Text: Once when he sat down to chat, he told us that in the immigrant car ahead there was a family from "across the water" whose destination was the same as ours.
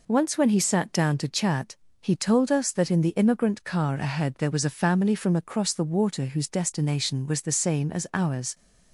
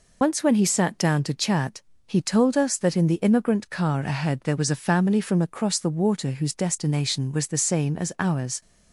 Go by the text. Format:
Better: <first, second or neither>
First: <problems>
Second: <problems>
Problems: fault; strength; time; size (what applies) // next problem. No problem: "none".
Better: first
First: none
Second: loses the start of "Once"; at 0.2 s; 85 ms